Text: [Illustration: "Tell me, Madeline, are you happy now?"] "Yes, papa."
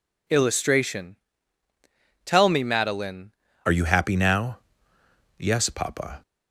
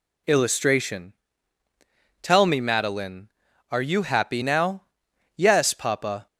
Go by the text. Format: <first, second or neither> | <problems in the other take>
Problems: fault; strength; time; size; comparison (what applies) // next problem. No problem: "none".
second | changes voice at "are"; from 3.6 s on; 2.6 s long